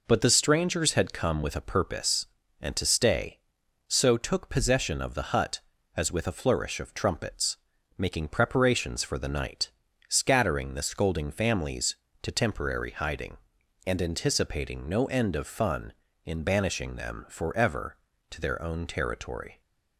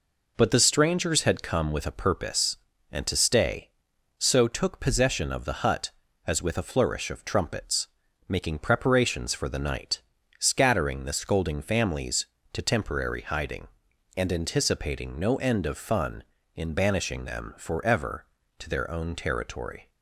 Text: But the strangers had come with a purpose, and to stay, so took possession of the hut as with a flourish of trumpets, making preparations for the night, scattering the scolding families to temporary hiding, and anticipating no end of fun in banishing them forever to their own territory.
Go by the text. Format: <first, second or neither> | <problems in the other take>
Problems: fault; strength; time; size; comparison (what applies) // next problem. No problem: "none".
neither | none